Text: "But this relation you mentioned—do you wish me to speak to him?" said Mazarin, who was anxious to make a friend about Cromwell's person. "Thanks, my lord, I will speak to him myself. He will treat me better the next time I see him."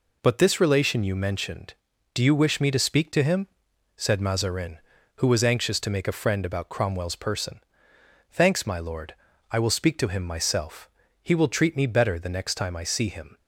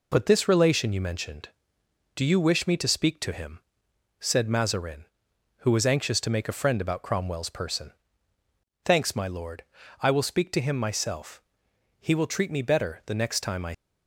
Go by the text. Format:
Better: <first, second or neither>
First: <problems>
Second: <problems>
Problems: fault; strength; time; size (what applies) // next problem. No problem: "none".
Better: first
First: none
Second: stops before "see him"; at 13.7 s